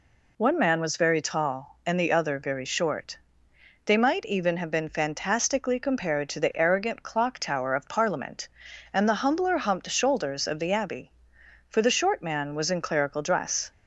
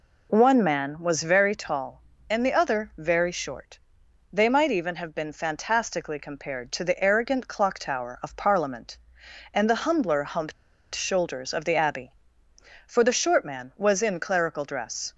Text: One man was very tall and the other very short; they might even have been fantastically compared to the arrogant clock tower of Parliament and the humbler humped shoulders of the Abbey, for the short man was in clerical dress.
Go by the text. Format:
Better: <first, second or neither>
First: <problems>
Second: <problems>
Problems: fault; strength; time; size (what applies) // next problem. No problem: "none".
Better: first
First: none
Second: pauses between "humped" and "shoulders"; at 10.5 s; 0.41 s long